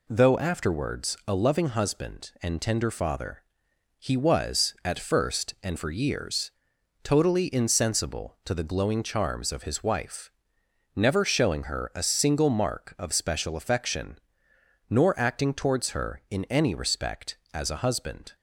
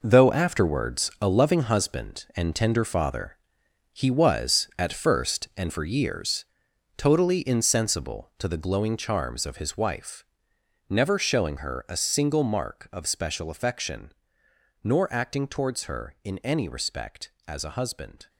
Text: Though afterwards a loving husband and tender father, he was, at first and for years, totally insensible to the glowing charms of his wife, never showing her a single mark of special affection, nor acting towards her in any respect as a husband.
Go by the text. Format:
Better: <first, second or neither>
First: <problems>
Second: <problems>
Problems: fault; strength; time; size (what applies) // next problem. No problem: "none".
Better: first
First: none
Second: gets quieter; strong; throughout; 10 dB